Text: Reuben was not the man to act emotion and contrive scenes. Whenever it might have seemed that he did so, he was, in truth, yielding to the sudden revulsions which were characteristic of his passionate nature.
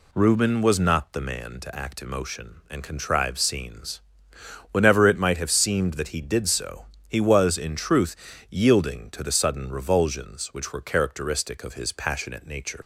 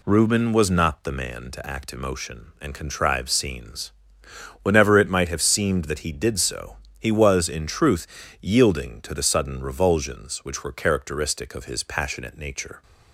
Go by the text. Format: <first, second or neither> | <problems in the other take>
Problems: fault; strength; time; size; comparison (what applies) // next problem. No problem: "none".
second | leaves "nature" unfinished; at 12.8 s; 90 ms